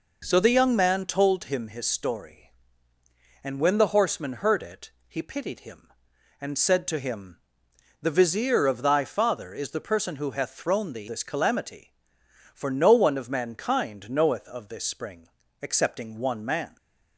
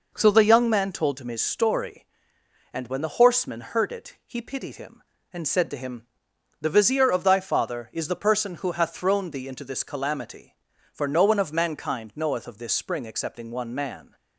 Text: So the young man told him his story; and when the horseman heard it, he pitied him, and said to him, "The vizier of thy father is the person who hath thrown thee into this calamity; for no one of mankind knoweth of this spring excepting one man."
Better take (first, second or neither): second